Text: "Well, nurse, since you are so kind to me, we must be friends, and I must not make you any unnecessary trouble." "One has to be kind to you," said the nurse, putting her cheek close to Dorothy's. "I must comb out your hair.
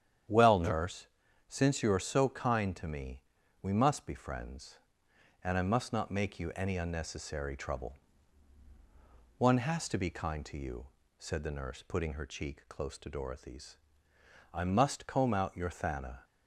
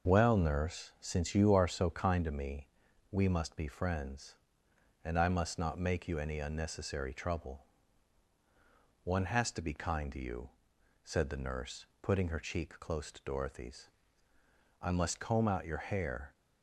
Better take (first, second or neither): second